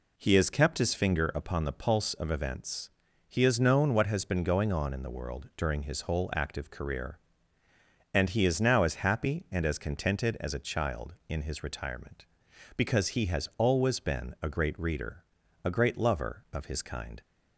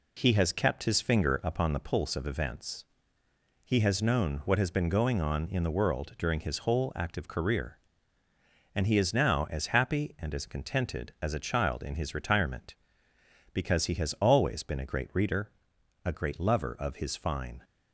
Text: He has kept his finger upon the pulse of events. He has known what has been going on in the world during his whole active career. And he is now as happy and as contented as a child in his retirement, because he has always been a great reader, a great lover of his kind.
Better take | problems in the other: first | says "fine" for "kind"; at 17.1 s

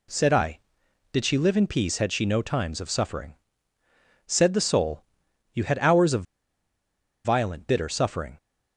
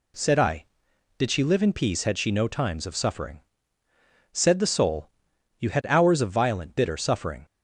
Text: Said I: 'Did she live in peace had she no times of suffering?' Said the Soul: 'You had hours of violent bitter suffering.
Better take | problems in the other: second | pauses between "of" and "violent"; at 6.2 s; 1.0 s long

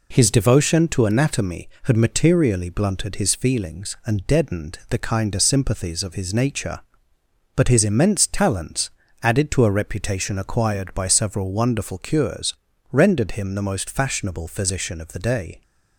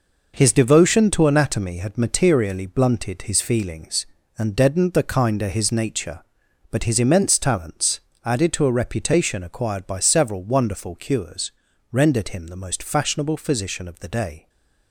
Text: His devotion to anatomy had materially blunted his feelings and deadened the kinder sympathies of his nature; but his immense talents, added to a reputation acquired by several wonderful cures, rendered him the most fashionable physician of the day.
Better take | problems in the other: first | skips "sympathies of"; at 5.4 s // stays silent after the last word; slight; from 14.3 s on; 0.6 s long

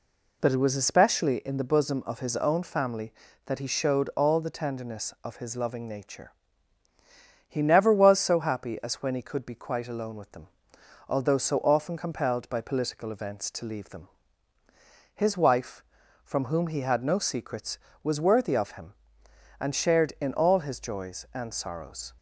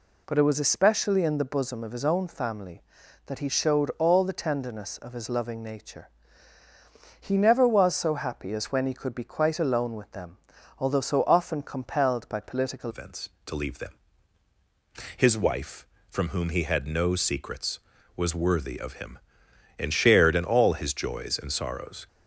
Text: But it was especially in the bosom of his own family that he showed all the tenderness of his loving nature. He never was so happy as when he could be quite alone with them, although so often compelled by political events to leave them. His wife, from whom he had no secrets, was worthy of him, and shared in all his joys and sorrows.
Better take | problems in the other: first | changes voice at "events"; from 12.8 s on; 9.2 s long

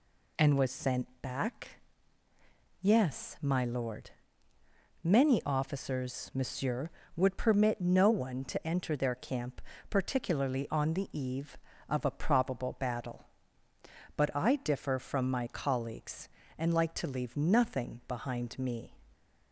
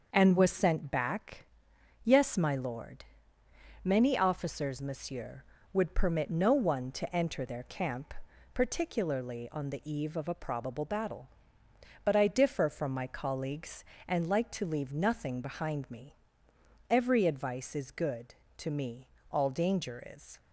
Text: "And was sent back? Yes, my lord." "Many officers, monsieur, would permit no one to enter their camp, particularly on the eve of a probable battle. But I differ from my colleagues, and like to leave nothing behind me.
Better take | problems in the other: first | starts louder than the rest; until 1.1 s; 6.5 dB // goes on to say "Every advice is good to me all danger is"; strong; from 16.9 s on; 3.4 s long

